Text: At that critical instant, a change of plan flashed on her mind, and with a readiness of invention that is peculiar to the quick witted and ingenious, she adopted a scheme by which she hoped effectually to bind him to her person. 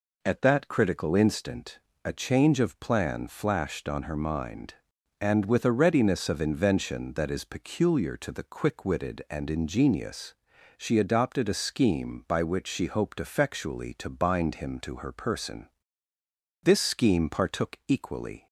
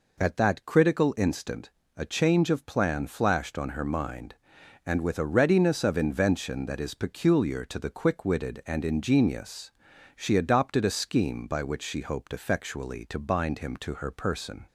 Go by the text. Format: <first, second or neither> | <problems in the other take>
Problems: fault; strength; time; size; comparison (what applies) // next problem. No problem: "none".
second | goes on to say "This scheme partook equally"; strong; from 16.6 s on; 1.8 s long